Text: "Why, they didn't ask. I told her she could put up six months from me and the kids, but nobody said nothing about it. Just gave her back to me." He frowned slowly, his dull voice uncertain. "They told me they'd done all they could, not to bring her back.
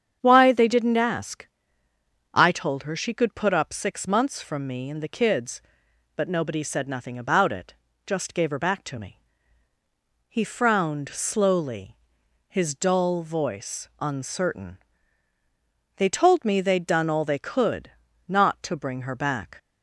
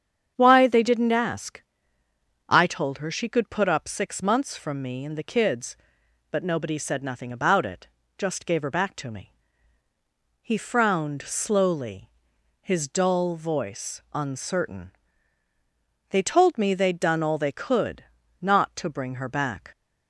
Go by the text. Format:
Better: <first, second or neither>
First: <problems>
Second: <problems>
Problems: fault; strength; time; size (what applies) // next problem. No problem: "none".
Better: neither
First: starts louder than the rest; strong; until 1.2 s; 8 dB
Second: starts louder than the rest; strong; until 1.3 s; 8 dB